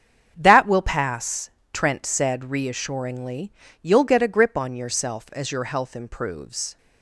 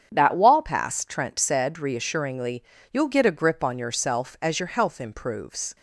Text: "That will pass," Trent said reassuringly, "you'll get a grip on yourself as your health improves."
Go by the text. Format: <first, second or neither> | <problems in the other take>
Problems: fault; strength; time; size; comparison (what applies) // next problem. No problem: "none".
first | starts louder than the rest; strong; until 1.1 s; 8 dB; strong in the first // says "wall" for "will"; at 0.3 s